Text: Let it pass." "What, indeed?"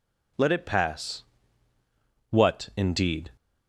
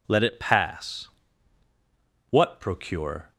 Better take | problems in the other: first | says "procure" for "indeed"; at 2.6 s

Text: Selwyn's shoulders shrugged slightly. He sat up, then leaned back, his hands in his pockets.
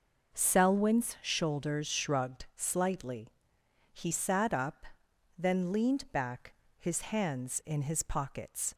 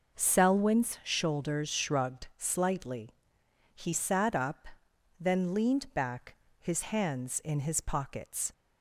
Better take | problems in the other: neither | none

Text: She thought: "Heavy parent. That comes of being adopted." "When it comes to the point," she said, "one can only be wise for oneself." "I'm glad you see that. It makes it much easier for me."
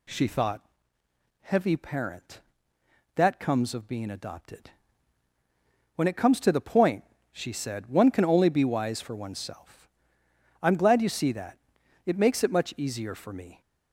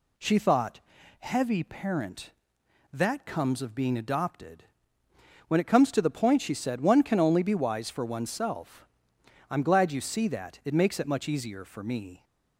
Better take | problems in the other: neither | none

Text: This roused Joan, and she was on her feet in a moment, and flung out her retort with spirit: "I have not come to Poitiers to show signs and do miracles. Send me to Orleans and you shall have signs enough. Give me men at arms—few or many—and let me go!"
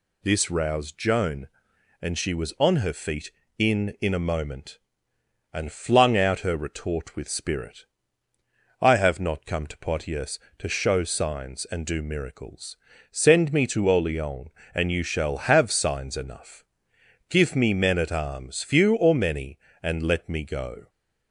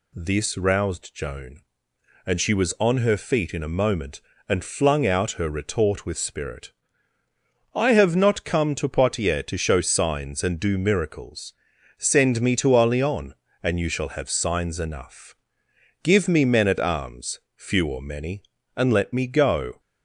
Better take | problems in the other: second | says "in" twice; at 4.0 s

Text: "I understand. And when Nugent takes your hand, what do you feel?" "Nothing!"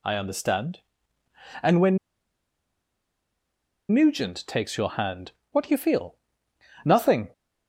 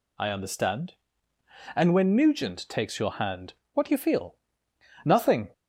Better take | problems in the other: second | pauses between "when" and "Nugent"; strong; at 1.9 s; 1.9 s long

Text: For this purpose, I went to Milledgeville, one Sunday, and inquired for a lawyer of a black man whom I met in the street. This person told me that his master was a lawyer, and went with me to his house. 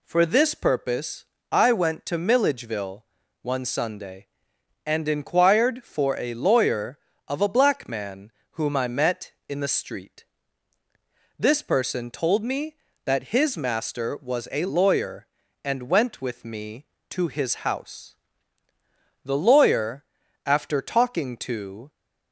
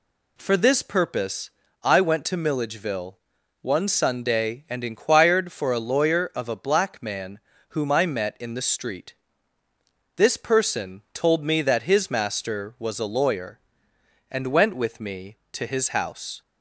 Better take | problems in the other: second | pauses between "man" and "whom"; slight; at 8.3 s; 0.20 s long; slight in the second // goes on to say "The lawyer after talking to"; strong; from 19.2 s on; 2.6 s long

